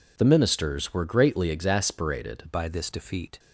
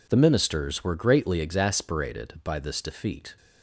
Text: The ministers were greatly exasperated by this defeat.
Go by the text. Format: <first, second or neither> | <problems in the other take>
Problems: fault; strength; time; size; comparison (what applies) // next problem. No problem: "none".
second | changes voice at "by"; from 2.5 s on; 0.8 s long